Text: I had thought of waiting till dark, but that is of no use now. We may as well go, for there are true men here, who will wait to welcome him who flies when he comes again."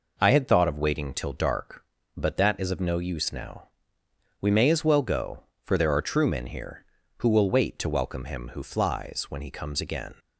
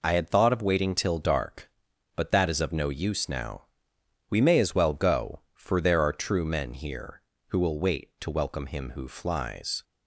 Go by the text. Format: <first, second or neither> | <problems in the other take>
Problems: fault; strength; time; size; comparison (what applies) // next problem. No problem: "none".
first | stops before "when he comes again"; at 9.8 s